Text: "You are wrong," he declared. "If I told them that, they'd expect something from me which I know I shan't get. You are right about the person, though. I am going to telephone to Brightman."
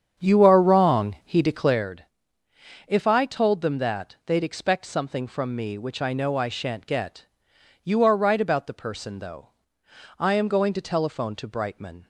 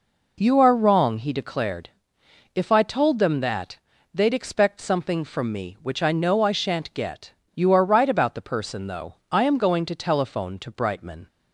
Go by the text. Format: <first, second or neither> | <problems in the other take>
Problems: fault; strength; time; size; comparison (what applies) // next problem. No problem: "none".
second | starts louder than the rest; strong; until 1.9 s; 8 dB